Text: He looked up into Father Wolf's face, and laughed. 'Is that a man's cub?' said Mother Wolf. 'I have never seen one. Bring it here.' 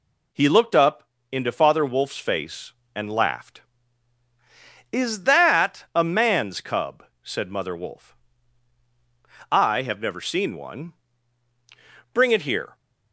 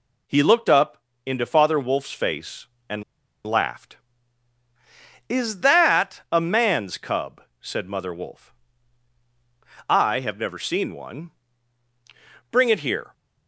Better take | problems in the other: first | pauses between "up" and "into"; slight; at 0.9 s; 0.28 s long; slight in the first // pauses between "and" and "laughed"; at 3.0 s; 0.43 s long

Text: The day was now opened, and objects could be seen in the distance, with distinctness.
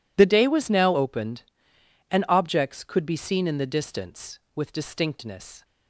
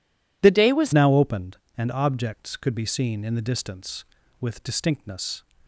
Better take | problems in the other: first | changes voice at "now"; from 0.9 s on; 4.5 s long

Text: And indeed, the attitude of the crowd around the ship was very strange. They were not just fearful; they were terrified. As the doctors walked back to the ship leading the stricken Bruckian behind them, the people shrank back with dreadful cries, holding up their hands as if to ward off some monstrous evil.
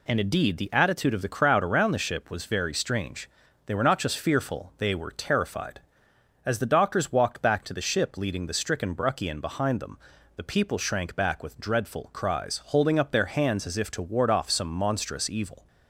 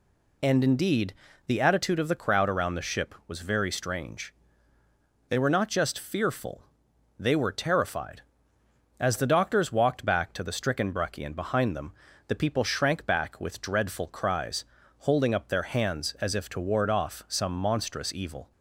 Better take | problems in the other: first | skips "the ship leading"; at 10.4 s

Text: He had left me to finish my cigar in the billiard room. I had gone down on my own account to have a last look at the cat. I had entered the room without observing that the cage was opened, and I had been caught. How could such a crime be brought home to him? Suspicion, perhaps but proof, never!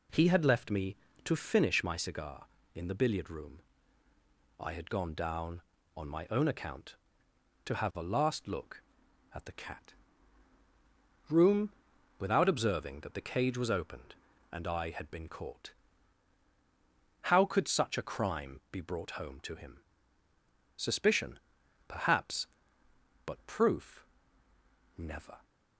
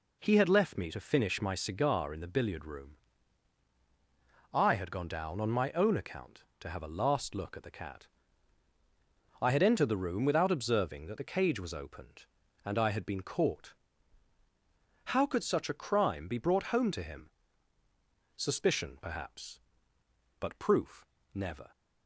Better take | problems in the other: second | skips "I had entered the"; at 10.6 s // pauses between "room" and "without"; noticeable; at 11.7 s; 0.48 s long

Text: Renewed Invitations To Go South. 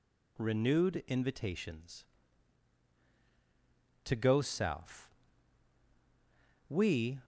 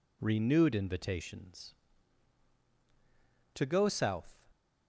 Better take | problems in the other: second | goes on to say "We"; from 6.6 s on; 0.52 s long

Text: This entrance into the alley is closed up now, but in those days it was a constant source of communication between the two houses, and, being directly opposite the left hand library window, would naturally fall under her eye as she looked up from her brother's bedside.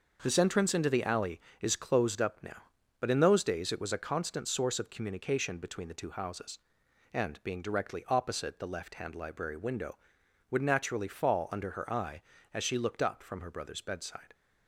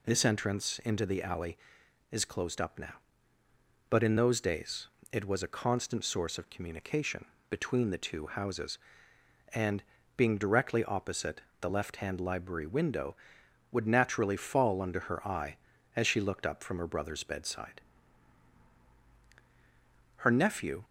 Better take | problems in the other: first | pauses between "days" and "it"; slight; at 4.8 s; 0.24 s long // pauses between "communication" and "between"; slight; at 7.2 s; 0.24 s long // pauses between "opposite" and "the"; slight; at 11.3 s; 0.22 s long // goes on to say "Her nephew"; noticeable; from 20.1 s on; 0.68 s long

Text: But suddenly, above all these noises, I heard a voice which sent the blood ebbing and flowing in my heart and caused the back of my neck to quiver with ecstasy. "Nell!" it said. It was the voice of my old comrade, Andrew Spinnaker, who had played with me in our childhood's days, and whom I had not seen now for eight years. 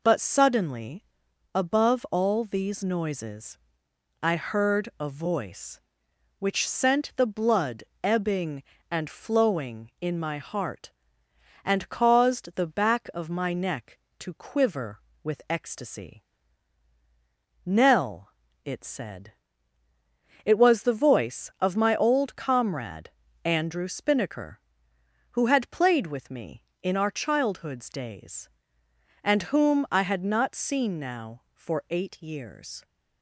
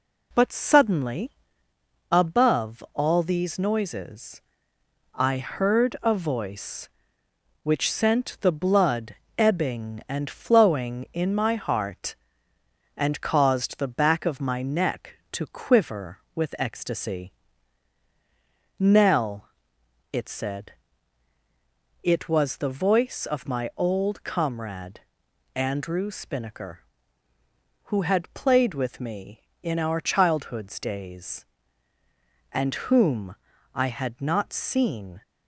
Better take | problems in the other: first | pauses between "blood" and "ebbing"; slight; at 9.1 s; 0.22 s long; slight in the first // pauses between "whom" and "I"; at 33.3 s; 0.38 s long // stops before "now for eight years"; at 35.2 s

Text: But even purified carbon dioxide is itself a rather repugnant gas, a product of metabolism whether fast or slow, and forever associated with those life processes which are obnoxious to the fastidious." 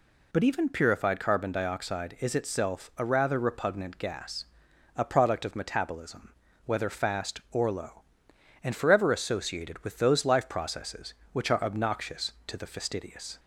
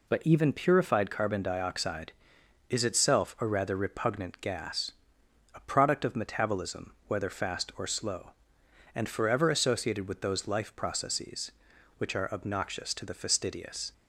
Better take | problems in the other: second | pauses between "metabolism" and "whether"; slight; at 6.3 s; 0.32 s long // says "low" for "slow"; at 7.7 s

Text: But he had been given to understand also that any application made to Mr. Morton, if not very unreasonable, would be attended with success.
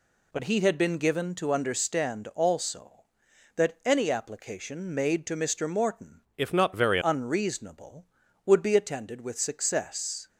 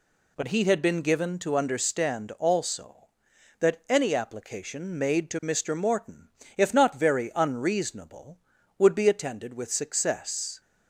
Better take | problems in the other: second | changes voice from "if" to "very"; from 6.3 to 6.9 s; 0.6 s long

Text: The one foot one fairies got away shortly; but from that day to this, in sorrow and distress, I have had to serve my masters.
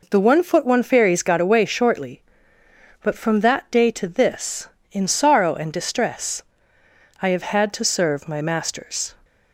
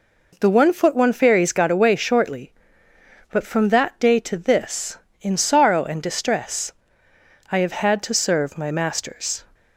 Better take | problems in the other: neither | none

